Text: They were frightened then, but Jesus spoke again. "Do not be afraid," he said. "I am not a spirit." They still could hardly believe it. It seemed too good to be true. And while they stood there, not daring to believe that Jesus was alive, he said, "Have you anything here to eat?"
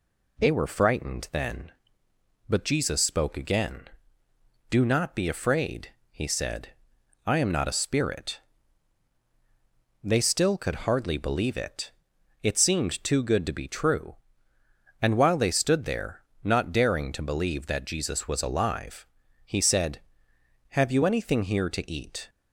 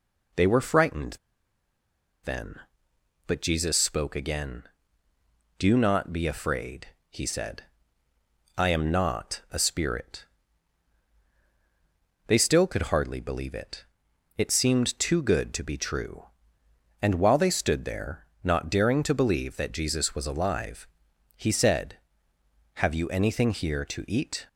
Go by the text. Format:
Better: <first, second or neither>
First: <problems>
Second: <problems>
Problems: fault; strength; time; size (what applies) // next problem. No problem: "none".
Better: first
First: none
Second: pauses between "frightened" and "then"; at 1.1 s; 1.0 s long